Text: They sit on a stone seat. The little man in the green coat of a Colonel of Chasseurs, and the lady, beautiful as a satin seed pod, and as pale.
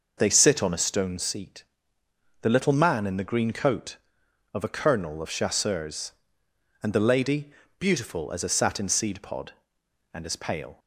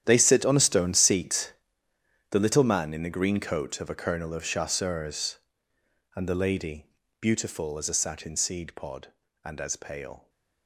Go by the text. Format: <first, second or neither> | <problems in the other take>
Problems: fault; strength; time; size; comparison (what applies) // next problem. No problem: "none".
first | gets quieter; strong; throughout; 15 dB